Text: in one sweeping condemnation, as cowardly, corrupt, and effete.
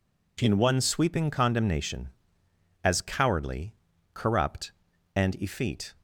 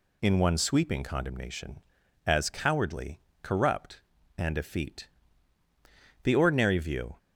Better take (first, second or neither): first